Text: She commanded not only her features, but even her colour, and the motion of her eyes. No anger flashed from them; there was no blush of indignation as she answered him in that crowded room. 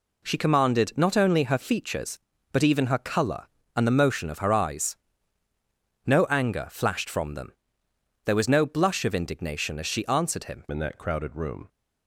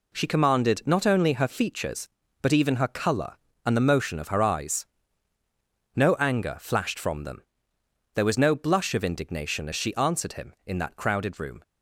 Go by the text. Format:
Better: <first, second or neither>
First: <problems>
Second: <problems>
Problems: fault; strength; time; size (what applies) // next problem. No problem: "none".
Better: second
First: changes voice at "in"; from 10.7 s on; 0.9 s long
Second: none